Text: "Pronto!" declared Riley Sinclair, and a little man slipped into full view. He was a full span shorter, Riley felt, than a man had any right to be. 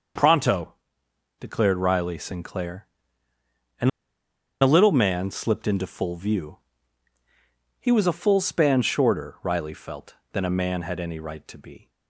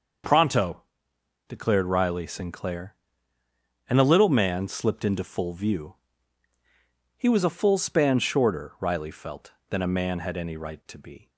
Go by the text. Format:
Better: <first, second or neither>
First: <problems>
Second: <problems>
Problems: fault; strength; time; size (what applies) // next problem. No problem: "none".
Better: second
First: starts louder than the rest; noticeable; until 1.8 s; 6 dB // pauses between "and" and "a"; noticeable; at 3.8 s; 0.71 s long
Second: none